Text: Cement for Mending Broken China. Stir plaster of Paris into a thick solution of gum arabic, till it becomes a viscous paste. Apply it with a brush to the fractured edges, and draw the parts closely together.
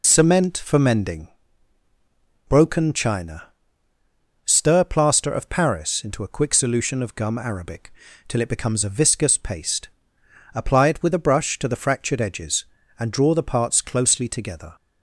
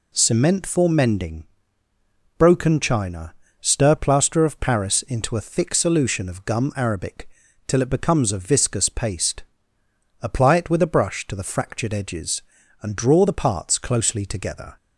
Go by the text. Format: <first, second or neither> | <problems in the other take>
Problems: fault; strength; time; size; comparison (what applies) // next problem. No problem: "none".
second | pauses between "Mending" and "Broken"; at 1.2 s; 1.1 s long; noticeable in the second // says "quick" for "thick"; at 6.3 s